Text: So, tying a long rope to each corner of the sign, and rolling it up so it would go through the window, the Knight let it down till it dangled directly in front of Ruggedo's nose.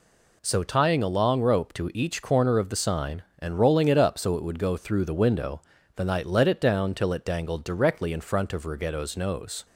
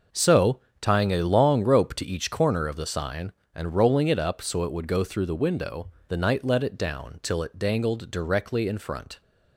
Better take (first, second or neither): first